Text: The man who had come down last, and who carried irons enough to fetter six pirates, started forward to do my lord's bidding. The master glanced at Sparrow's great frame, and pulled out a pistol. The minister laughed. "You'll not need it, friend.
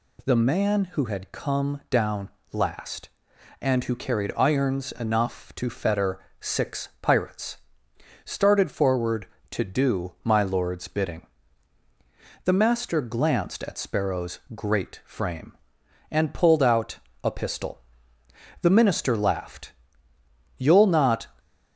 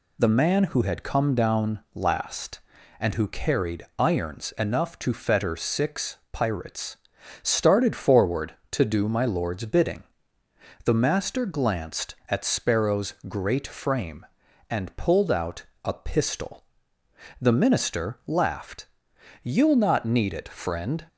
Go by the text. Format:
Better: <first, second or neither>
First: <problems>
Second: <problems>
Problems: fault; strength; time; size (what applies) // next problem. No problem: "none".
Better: second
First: pauses between "down" and "last"; slight; at 2.2 s; 0.24 s long // pauses between "fetter" and "six"; slight; at 6.2 s; 0.20 s long // pauses between "out" and "a"; slight; at 16.9 s; 0.26 s long // stops before "need it friend"; at 21.3 s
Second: pauses between "out" and "a"; slight; at 15.6 s; 0.18 s long